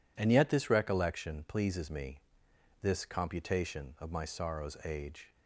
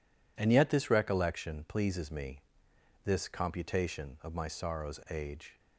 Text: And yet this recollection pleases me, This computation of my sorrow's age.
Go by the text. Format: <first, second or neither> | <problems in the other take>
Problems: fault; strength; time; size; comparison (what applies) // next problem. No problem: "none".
neither | none